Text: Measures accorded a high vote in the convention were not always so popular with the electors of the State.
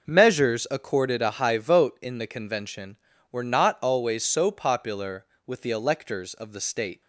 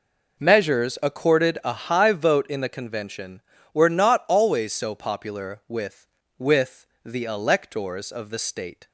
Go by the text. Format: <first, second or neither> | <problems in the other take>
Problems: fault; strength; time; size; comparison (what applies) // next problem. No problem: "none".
first | says "with" twice; at 6.3 s